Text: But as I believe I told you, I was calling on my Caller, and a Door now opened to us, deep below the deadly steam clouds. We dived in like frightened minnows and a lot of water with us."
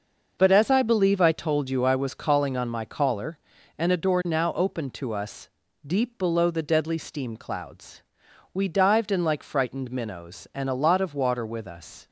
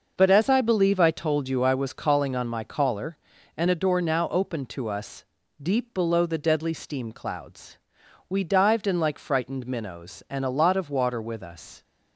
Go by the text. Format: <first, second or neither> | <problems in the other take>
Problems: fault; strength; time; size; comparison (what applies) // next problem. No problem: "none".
neither | none